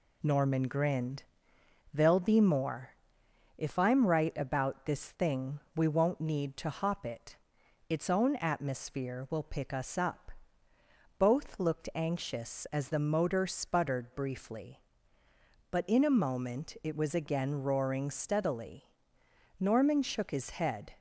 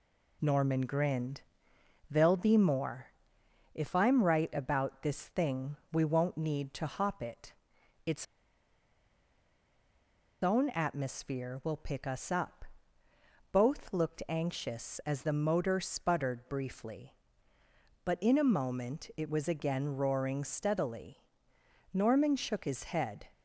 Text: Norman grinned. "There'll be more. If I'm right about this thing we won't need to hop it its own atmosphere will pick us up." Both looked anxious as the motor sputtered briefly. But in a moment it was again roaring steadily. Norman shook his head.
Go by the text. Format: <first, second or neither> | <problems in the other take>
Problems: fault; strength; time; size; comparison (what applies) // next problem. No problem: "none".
first | pauses between "thing" and "we"; slight; at 5.7 s; 0.16 s long; slight in the first // pauses between "it" and "its"; noticeable; at 7.5 s; 0.54 s long; noticeable in the first // pauses between "its" and "own"; strong; at 8.2 s; 2.1 s long